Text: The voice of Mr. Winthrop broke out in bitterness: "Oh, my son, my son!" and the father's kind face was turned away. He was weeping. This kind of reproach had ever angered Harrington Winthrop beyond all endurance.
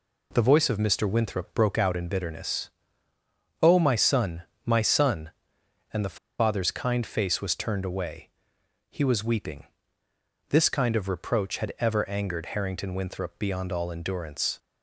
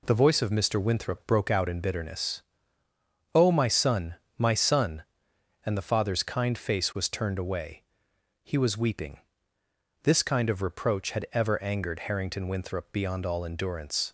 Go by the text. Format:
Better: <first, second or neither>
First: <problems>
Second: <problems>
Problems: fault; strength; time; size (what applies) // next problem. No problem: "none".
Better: second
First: pauses between "the" and "father's"; slight; at 6.1 s; 0.23 s long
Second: none